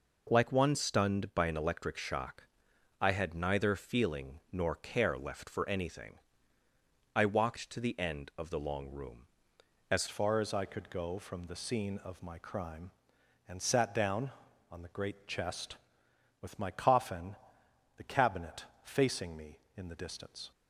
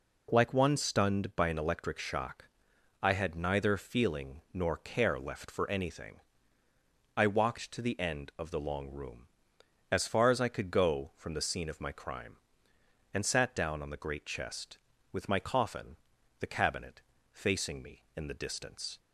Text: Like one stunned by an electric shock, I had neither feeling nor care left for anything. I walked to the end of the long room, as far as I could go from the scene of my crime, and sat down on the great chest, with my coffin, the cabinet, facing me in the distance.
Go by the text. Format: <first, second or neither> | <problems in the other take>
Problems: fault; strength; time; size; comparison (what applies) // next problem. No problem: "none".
second | changes voice at "far"; from 10.0 s on; 10.5 s long